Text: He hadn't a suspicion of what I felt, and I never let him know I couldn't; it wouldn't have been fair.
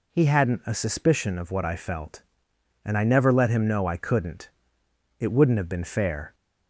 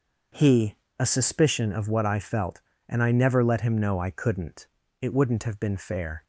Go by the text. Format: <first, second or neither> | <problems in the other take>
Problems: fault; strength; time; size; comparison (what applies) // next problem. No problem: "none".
first | starts louder than the rest; until 1.6 s; 6 dB // skips "hadn't"; at 0.8 s